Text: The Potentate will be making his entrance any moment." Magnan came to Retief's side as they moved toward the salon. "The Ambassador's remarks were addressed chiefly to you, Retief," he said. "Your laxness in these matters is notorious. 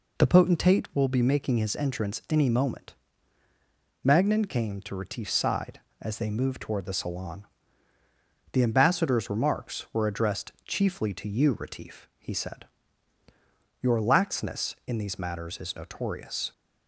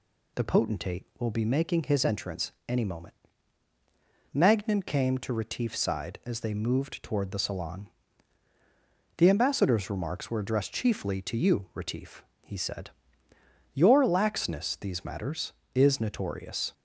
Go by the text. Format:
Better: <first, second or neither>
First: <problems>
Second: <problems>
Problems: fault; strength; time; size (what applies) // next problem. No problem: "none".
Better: first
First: none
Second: pauses between "entrance" and "any"; slight; at 2.5 s; 0.16 s long // skips "in"; at 14.7 s